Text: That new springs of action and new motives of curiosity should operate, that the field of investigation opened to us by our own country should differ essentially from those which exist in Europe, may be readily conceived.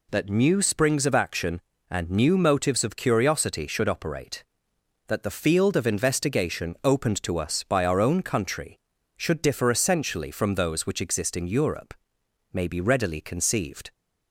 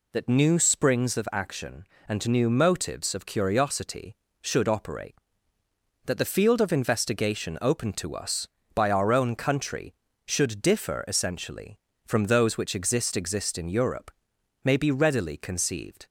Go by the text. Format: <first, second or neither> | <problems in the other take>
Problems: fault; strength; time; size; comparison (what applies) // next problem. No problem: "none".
first | says "exist" twice; at 13.1 s